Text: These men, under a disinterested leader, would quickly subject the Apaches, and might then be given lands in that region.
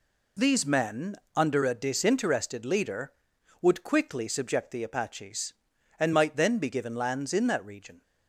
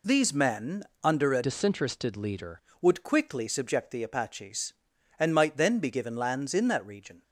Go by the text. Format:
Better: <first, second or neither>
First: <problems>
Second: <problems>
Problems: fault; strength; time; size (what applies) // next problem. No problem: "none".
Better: first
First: none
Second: changes voice from "disinterested" to "leader"; from 1.4 to 2.5 s; 1.1 s long